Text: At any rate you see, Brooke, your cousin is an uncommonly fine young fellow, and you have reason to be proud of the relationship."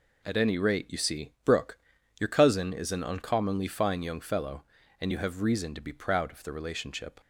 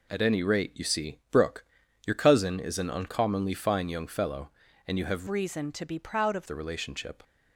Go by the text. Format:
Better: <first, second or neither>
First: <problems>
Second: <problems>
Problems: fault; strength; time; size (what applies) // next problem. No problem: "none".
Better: first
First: none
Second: changes voice from "reason" to "of"; from 5.2 to 6.4 s; 1.2 s long